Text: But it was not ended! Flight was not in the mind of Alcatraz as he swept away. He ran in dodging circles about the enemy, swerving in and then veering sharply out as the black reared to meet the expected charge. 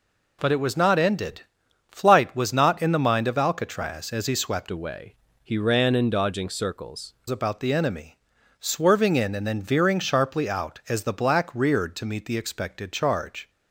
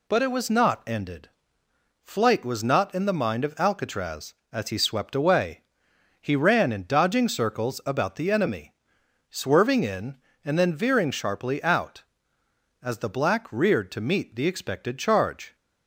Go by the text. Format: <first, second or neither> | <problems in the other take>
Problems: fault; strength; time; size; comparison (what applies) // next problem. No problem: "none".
second | changes voice from "away" to "circles"; from 4.7 to 7.1 s; 2.4 s long